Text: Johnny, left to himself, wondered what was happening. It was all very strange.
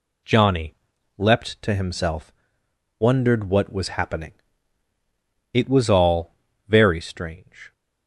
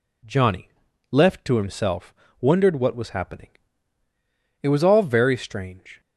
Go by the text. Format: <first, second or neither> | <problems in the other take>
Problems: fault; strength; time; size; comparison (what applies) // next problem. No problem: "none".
second | says "leapt" for "left"; at 1.1 s // pauses between "all" and "very"; slight; at 6.3 s; 0.32 s long